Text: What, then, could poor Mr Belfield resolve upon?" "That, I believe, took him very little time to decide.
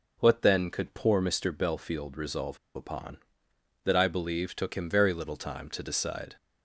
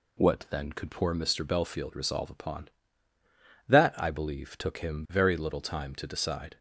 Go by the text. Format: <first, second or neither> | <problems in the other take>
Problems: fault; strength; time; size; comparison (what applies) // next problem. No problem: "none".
second | pauses between "resolve" and "upon"; slight; at 2.5 s; 0.18 s long